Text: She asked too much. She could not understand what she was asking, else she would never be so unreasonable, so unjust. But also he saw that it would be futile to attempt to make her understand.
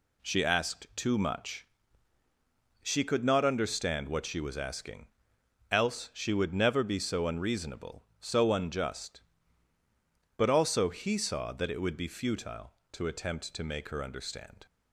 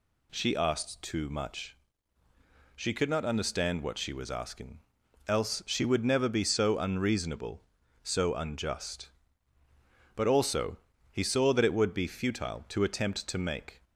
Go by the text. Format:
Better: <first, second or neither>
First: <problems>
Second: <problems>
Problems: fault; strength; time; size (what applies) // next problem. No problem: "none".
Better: first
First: none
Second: pauses between "also" and "he"; slight; at 10.7 s; 0.36 s long // stops before "her understand"; at 13.8 s